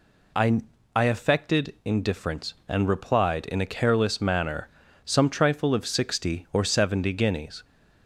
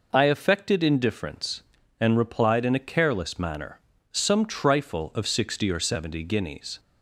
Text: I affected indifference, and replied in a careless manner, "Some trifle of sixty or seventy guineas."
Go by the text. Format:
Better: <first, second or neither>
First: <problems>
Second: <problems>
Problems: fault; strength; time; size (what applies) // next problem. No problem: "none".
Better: second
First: says "I" twice; at 0.9 s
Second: none